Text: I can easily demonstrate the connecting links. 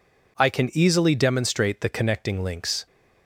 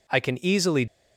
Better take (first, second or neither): first